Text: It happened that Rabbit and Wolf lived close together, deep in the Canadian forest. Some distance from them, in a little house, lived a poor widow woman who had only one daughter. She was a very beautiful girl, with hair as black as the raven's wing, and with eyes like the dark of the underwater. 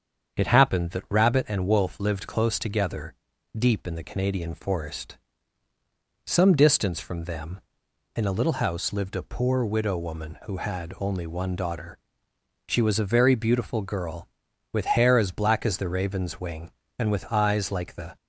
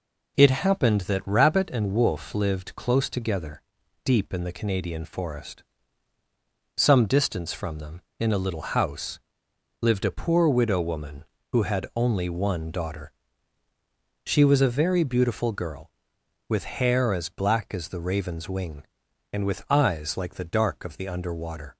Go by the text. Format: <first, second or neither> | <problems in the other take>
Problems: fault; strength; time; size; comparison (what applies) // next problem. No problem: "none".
second | starts louder than the rest; strong; until 1.4 s; 7 dB // stops before "dark of the underwater"; at 18.1 s